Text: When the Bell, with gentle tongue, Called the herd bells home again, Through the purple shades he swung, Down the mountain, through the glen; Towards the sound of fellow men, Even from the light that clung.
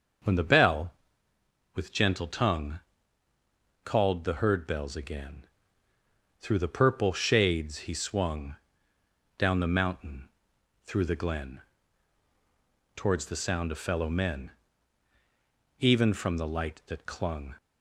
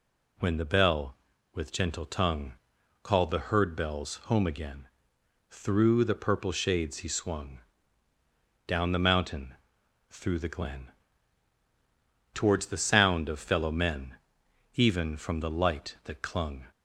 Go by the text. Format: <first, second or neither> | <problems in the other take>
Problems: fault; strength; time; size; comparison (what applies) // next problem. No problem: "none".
second | starts louder than the rest; until 2.0 s; 6.5 dB // skips "home"; at 4.9 s